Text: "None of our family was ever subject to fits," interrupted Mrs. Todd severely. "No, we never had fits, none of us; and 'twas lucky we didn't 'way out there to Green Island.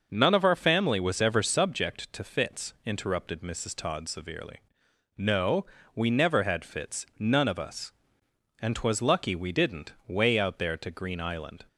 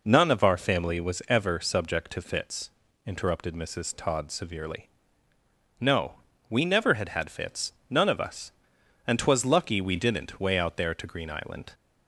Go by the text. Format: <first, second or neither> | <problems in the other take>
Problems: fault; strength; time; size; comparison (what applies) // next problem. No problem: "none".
first | says "had" twice; at 7.0 s